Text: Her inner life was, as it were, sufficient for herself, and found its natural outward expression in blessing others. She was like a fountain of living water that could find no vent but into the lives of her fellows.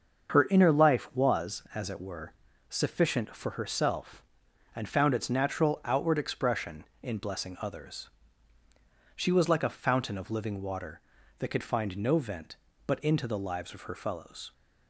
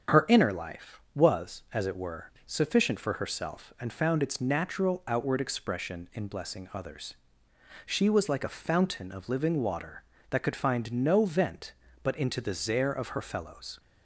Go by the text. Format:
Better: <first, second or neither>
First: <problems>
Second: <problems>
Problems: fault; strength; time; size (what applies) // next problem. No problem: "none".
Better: first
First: starts louder than the rest; until 1.3 s; 6.5 dB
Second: starts louder than the rest; strong; until 1.2 s; 7.5 dB // says "zare" for "lives"; at 12.5 s